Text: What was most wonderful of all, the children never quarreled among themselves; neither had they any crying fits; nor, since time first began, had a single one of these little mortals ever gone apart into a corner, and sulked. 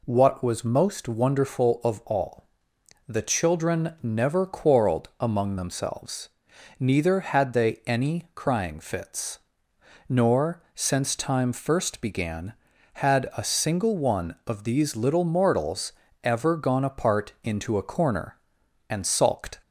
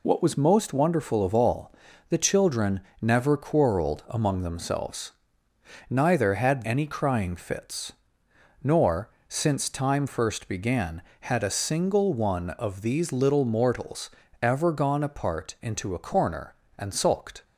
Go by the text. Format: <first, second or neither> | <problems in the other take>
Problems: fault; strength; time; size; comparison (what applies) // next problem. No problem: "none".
first | pauses between "children" and "never"; slight; at 2.7 s; 0.22 s long // skips "they"; at 6.6 s // pauses between "mortals" and "ever"; slight; at 14.1 s; 0.32 s long; slight in the first